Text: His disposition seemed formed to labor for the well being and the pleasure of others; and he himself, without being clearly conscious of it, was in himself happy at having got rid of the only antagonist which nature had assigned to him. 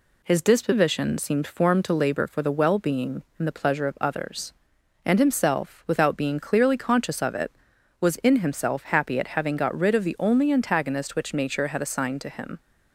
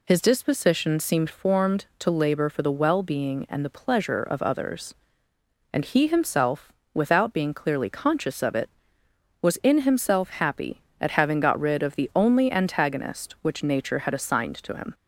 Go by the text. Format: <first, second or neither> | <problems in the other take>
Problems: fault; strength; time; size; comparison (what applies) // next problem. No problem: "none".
second | skips "he"; at 5.1 s